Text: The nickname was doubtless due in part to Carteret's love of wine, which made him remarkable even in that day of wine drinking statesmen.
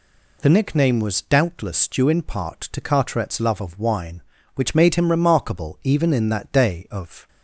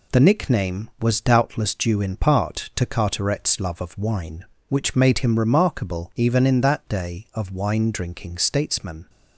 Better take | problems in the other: second | stops before "wine drinking statesmen"; at 7.2 s

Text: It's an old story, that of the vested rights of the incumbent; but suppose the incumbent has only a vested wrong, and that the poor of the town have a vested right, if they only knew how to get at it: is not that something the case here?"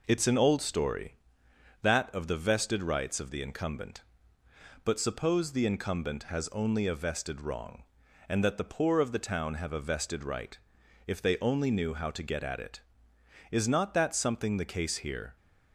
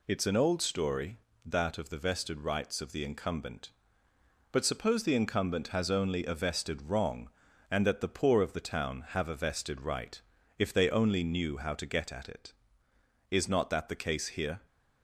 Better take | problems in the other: first | skips "something"; at 13.8 s

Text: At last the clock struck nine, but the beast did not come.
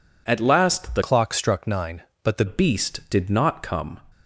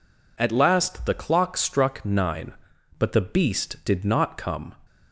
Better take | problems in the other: second | changes voice from "clock" to "the"; from 1.0 to 2.4 s; 1.4 s long

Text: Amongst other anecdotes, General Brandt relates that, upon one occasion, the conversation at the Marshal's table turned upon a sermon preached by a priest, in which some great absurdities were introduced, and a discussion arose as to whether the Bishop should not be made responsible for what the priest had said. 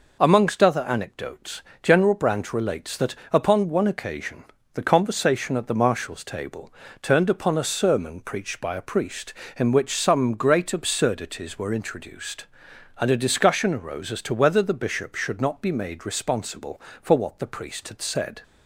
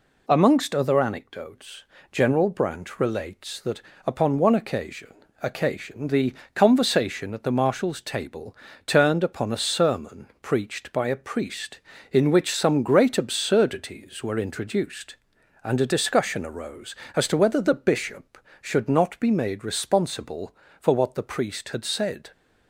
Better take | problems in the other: first | says "occasion" twice; at 5.4 s // pauses between "the" and "conversation"; slight; at 6.3 s; 0.22 s long // pauses between "table" and "turned"; slight; at 8.5 s; 0.30 s long; slight in the first

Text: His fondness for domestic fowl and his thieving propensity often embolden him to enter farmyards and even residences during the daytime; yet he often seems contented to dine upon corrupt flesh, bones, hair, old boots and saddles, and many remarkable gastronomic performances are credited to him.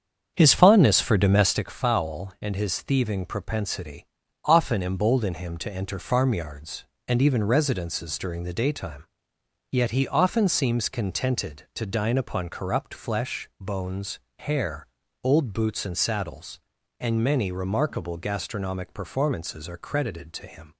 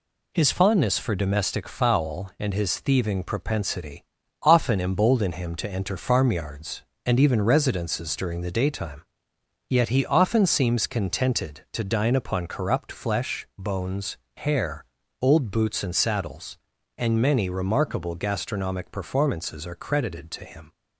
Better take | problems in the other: second | starts louder than the rest; strong; until 1.8 s; 7.5 dB // pauses between "propensity" and "often"; at 4.0 s; 0.40 s long; also in the second

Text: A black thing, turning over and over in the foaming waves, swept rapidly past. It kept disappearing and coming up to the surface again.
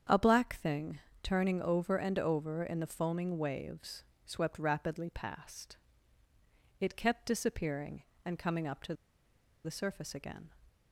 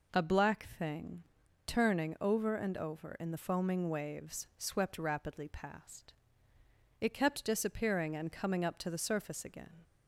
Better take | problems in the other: second | starts louder than the rest; strong; until 1.3 s; 8 dB // pauses between "to" and "the"; noticeable; at 8.9 s; 0.70 s long

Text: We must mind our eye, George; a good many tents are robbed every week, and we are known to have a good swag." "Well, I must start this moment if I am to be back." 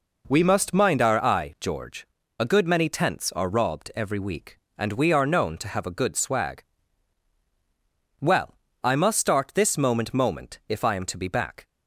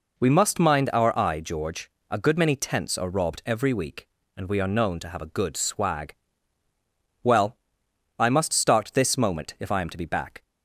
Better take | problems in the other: second | says "moment" twice; at 10.1 s

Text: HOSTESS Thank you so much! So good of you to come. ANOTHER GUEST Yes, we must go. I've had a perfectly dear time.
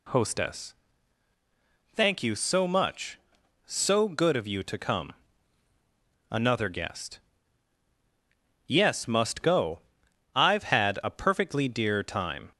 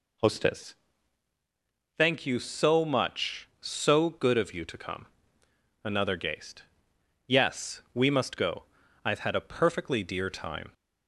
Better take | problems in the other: second | pauses between "HOSTESS" and "Thank"; at 0.7 s; 1.2 s long; also in the second // pauses between "GUEST" and "Yes"; strong; at 7.1 s; 1.4 s long; noticeable in the second // skips "we"; at 9.0 s

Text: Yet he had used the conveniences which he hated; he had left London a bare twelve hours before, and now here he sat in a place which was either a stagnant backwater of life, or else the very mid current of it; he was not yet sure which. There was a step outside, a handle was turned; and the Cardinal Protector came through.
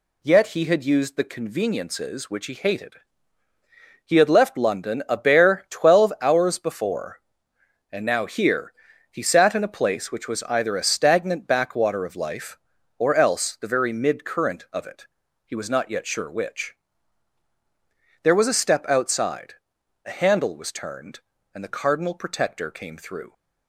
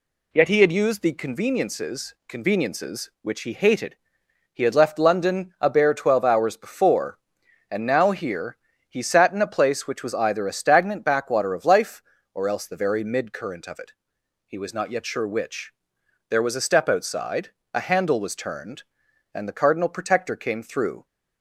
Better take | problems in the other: first | says "conveniences" twice; at 2.2 s // pauses between "here" and "he"; slight; at 8.5 s; 0.32 s long; also in the first

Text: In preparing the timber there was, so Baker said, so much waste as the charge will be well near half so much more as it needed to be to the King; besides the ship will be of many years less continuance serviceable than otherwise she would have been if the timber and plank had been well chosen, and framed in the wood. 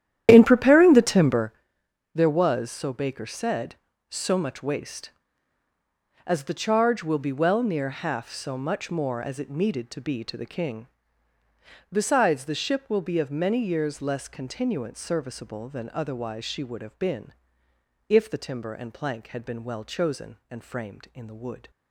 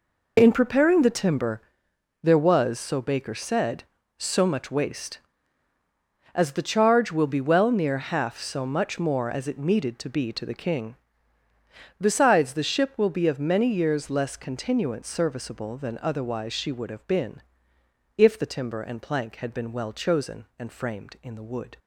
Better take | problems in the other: second | starts louder than the rest; strong; until 1.5 s; 11 dB // pauses between "timber" and "there"; noticeable; at 1.5 s; 0.62 s long; noticeable in the second // pauses between "been" and "if"; noticeable; at 17.3 s; 0.74 s long; noticeable in the second

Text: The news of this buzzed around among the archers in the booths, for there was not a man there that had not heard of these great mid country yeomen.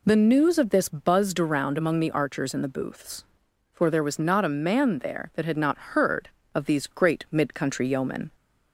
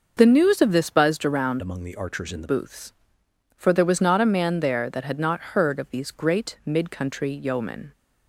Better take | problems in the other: first | changes voice from "among" to "the"; from 1.5 to 2.4 s; 0.9 s long

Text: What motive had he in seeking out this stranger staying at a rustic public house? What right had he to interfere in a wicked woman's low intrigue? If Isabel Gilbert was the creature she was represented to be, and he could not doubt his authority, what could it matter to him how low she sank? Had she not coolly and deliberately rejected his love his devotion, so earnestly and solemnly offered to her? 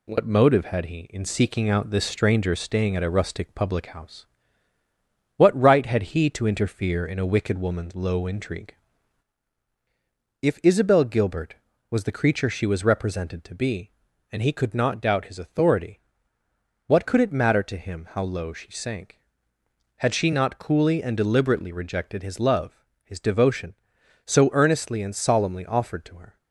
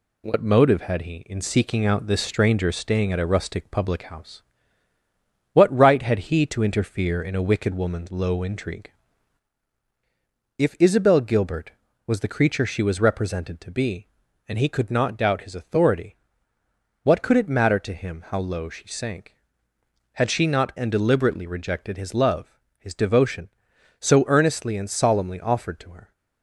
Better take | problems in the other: first | skips "coolly"; at 20.7 s // pauses between "love" and "his"; slight; at 22.4 s; 0.32 s long; slight in the first

